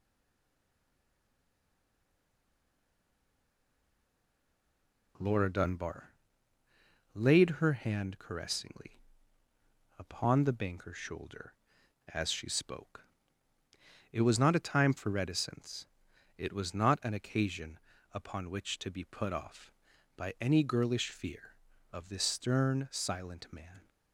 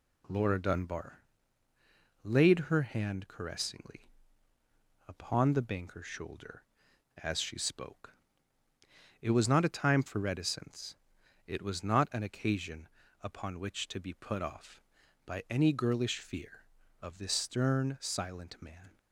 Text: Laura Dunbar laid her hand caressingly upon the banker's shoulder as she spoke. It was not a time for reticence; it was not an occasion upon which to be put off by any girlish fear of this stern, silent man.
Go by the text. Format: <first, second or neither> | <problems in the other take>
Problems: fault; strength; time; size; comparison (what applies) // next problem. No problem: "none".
second | stays silent before the first word; strong; until 5.1 s; 5.1 s long // pauses between "Dunbar" and "laid"; at 6.1 s; 1.0 s long; also in the second // pauses between "caressingly" and "upon"; noticeable; at 9.0 s; 0.98 s long; noticeable in the second // pauses between "occasion" and "upon"; slight; at 17.7 s; 0.34 s long; slight in the second